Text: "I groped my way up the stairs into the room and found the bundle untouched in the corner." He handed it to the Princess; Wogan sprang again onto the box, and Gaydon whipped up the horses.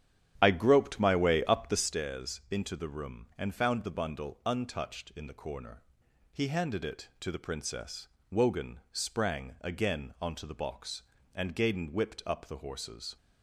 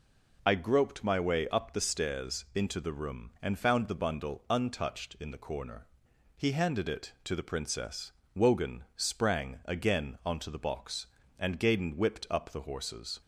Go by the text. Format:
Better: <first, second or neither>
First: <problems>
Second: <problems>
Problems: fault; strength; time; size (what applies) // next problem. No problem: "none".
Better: second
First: starts louder than the rest; strong; until 1.9 s; 9.5 dB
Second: none